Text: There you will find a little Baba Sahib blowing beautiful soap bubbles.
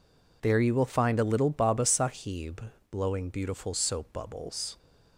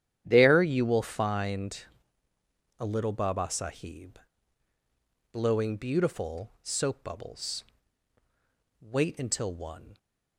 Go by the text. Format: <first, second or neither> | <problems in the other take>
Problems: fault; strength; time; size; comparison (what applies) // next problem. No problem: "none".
first | starts louder than the rest; strong; until 1.2 s; 10 dB // pauses between "find" and "a"; noticeable; at 1.8 s; 0.96 s long // pauses between "Sahib" and "blowing"; at 4.1 s; 1.1 s long; slight in the first // goes on to say "Wait until one"; noticeable; from 8.8 s on; 1.1 s long